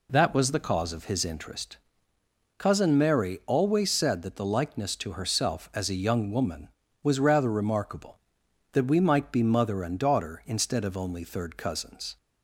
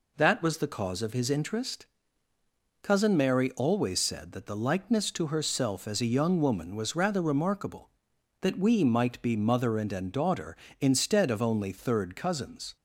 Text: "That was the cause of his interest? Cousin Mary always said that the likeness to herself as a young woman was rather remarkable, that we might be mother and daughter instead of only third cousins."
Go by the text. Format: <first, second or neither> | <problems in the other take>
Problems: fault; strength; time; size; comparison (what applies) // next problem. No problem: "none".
first | says "and" twice; at 9.9 s